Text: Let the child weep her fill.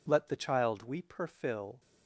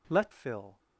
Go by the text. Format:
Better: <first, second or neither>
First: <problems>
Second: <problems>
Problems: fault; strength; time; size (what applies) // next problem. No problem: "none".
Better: first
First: none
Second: skips "the child weep her"; at 0.3 s